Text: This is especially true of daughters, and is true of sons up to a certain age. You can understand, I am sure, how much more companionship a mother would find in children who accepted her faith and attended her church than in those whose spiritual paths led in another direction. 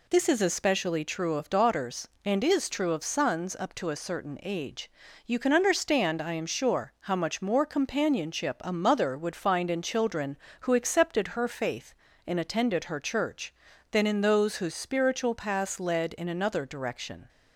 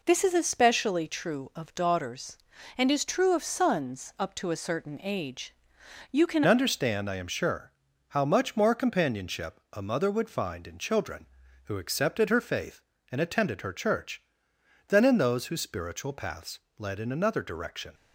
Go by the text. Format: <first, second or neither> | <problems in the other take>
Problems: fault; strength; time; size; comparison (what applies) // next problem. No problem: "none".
first | changes voice at "understand"; from 6.4 s on; 11.5 s long // pauses between "paths" and "led"; slight; at 16.5 s; 0.20 s long